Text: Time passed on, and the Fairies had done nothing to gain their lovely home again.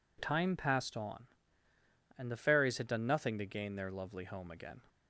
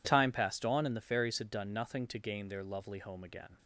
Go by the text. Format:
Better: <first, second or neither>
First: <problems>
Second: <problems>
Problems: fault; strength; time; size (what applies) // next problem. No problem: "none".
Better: neither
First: none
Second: none